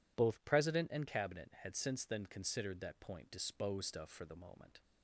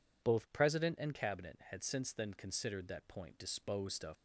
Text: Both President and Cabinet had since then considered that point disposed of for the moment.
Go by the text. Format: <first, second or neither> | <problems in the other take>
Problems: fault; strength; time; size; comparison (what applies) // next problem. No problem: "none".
first | stops before "for the moment"; at 4.1 s